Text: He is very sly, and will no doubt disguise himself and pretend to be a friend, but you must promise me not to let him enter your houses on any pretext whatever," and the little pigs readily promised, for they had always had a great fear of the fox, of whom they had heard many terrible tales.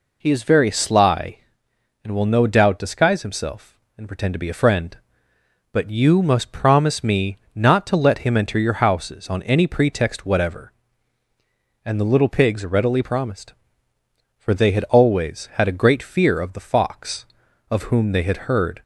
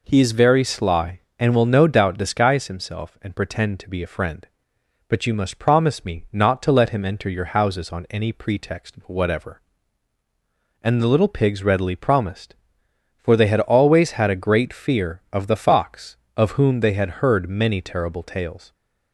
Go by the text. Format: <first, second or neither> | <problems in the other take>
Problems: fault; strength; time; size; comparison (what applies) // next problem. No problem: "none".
second | pauses between "me" and "not"; slight; at 7.3 s; 0.16 s long // stops before "many terrible tales"; at 18.8 s